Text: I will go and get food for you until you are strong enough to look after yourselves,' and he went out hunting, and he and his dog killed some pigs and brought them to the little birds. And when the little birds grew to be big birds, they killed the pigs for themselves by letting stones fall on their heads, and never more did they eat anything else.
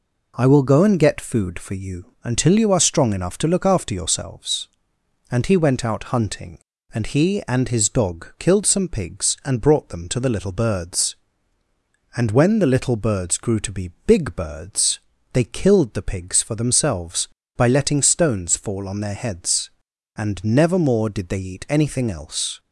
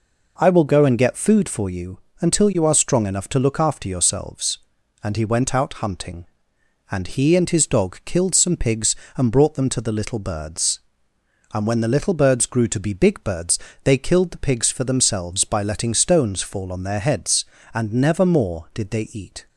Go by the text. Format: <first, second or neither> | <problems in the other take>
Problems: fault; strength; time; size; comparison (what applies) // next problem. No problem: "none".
first | pauses between "you" and "until"; slight; at 1.9 s; 0.22 s long // stops before "anything else"; at 19.4 s